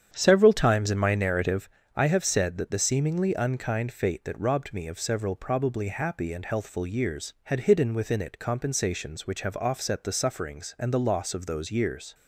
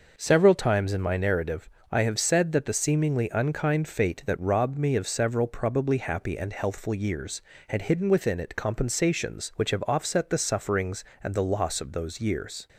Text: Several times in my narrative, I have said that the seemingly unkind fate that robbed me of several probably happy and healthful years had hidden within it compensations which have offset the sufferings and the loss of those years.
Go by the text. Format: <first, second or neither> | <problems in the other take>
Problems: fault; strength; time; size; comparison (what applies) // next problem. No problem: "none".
second | starts louder than the rest; strong; until 1.8 s; 8.5 dB